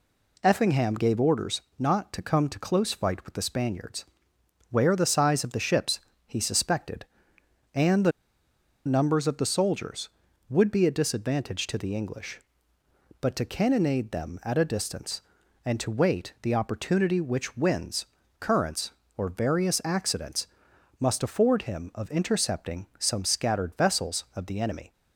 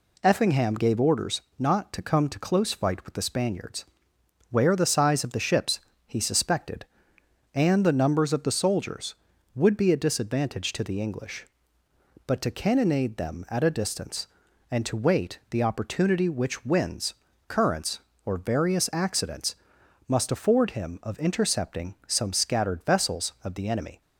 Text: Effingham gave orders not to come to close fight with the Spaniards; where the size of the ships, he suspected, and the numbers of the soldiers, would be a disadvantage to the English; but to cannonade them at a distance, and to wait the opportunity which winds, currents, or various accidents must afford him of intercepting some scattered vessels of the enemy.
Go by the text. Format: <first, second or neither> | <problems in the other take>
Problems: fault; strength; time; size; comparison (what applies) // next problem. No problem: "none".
second | pauses between "orders" and "not"; slight; at 1.6 s; 0.18 s long; slight in the second // pauses between "the" and "numbers"; noticeable; at 8.1 s; 0.75 s long // pauses between "accidents" and "must"; noticeable; at 20.4 s; 0.52 s long; noticeable in the second